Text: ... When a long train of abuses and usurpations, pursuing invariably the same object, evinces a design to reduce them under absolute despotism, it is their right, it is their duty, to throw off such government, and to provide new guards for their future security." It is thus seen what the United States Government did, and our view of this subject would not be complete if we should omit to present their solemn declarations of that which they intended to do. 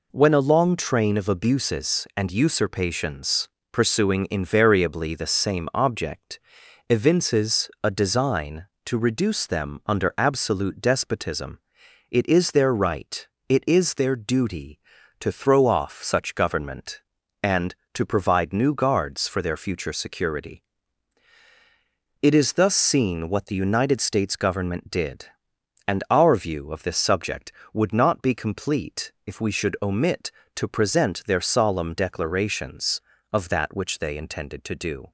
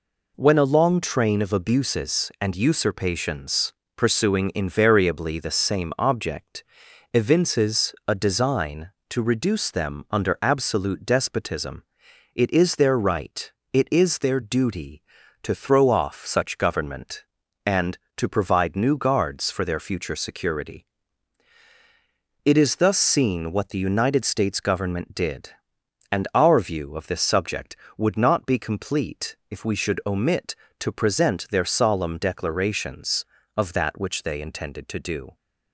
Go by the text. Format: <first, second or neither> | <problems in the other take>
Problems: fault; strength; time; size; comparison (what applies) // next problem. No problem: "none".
neither | none